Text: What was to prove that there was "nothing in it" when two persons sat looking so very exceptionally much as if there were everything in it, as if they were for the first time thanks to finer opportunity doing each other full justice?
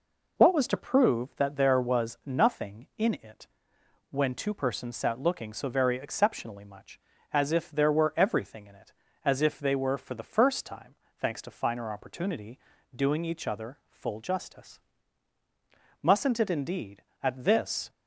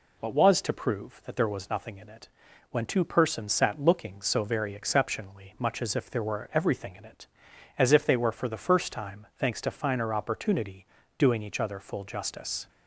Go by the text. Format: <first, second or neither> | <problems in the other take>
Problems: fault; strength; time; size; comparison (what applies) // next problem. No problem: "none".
second | pauses between "it" and "when"; noticeable; at 3.4 s; 0.64 s long; also in the second // pauses between "time" and "thanks"; slight; at 10.9 s; 0.24 s long // pauses between "opportunity" and "doing"; slight; at 12.5 s; 0.36 s long; slight in the second // goes on to say "Mustn't it indeed at this"; strong; from 16.0 s on; 1.8 s long